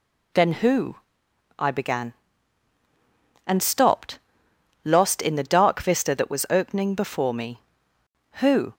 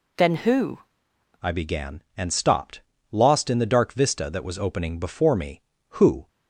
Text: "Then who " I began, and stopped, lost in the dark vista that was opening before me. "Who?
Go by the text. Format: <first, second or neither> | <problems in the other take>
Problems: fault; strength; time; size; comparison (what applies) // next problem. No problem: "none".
first | changes voice at "I"; from 1.4 s on; 4.8 s long